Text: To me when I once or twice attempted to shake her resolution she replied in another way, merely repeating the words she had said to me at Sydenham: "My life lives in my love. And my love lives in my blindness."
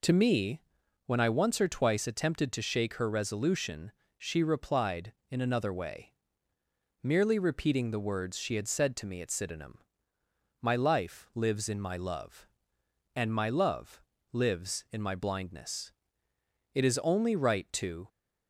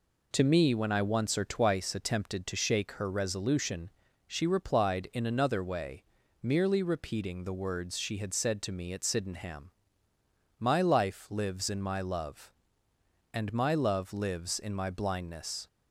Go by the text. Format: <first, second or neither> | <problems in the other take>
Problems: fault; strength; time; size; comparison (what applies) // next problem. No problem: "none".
second | pauses between "me" and "when"; noticeable; at 0.6 s; 0.46 s long // pauses between "resolution" and "she"; slight; at 3.9 s; 0.28 s long; slight in the second // pauses between "love" and "lives"; slight; at 14.0 s; 0.32 s long // goes on to say "It is only right to"; from 16.7 s on; 1.3 s long